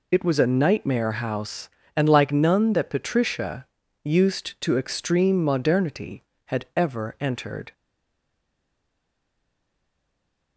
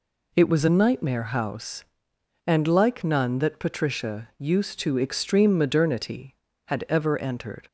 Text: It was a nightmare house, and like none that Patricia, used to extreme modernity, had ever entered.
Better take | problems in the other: second | stays silent after the last word; strong; from 7.7 s on; 2.8 s long

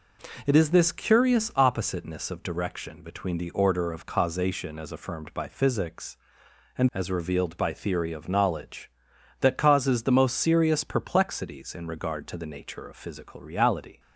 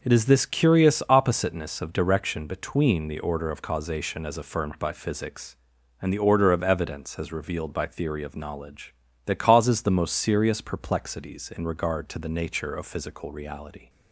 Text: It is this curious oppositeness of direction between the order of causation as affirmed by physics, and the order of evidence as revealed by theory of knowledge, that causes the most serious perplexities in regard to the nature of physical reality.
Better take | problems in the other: second | skips "the order of evidence"; at 6.9 s

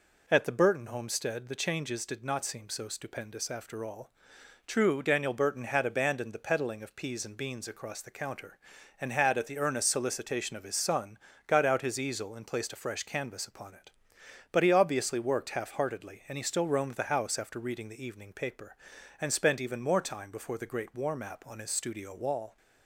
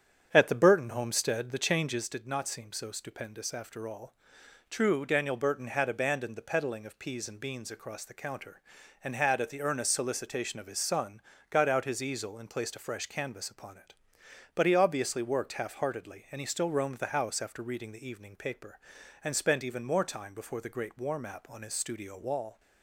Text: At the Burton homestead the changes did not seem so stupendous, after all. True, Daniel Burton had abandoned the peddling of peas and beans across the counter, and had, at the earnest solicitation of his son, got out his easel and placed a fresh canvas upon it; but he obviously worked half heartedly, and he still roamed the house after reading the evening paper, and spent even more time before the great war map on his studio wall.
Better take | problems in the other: first | starts louder than the rest; strong; until 2.2 s; 8 dB

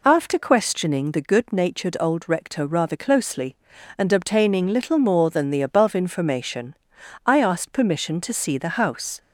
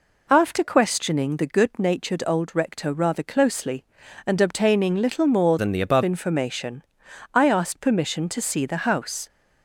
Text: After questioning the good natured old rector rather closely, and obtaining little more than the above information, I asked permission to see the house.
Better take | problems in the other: first | changes voice from "than" to "above"; from 5.5 to 6.0 s; 0.5 s long

